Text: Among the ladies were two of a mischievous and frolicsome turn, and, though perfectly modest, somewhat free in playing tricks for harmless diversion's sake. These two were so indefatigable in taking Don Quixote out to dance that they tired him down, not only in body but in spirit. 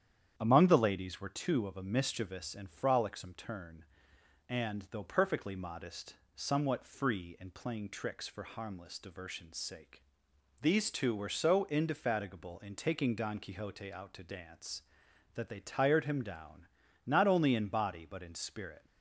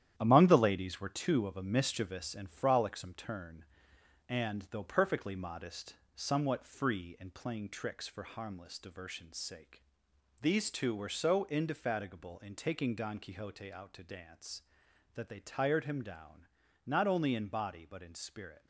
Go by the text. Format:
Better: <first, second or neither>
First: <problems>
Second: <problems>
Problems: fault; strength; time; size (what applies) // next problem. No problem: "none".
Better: first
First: starts louder than the rest; strong; until 1.3 s; 9 dB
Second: gets quieter; strong; throughout; 7 dB // starts louder than the rest; strong; until 1.1 s; 10.5 dB